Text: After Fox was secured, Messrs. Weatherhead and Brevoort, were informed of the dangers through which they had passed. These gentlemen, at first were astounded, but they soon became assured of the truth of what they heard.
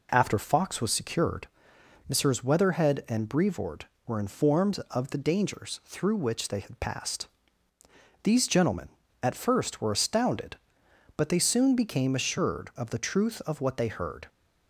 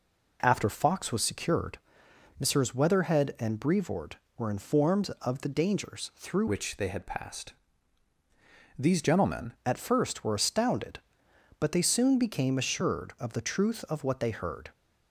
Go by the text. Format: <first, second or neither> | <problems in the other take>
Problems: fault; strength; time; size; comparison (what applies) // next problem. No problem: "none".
first | changes voice from "which" to "gentlemen"; from 6.4 to 9.5 s; 3.1 s long